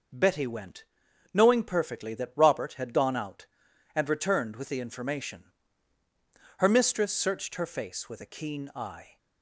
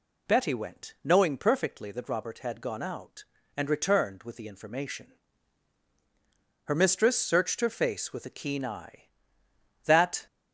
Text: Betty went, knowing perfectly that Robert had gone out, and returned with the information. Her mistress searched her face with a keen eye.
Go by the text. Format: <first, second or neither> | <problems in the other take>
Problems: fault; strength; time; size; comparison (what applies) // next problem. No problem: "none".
first | goes on to say "That"; slight; from 9.8 s on; 0.42 s long